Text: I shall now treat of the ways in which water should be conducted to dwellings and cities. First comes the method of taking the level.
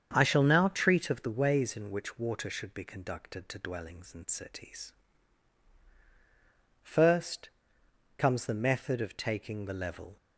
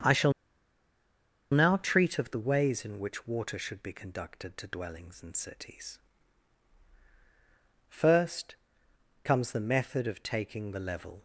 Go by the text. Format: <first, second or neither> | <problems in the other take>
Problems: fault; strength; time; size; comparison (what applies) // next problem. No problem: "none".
first | starts louder than the rest; strong; until 2.2 s; 7.5 dB; strong in the first // pauses between "shall" and "now"; at 0.3 s; 1.2 s long // pauses between "First" and "comes"; noticeable; at 8.5 s; 0.68 s long; noticeable in the first